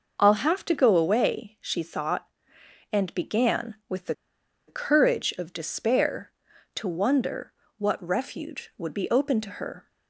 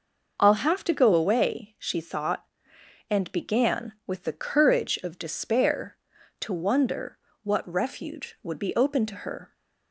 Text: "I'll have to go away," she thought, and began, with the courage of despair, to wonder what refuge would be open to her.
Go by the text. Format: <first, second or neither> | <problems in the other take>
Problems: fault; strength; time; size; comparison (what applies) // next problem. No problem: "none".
second | pauses between "the" and "courage"; noticeable; at 4.1 s; 0.54 s long // pauses between "wonder" and "what"; slight; at 7.5 s; 0.26 s long; slight in the second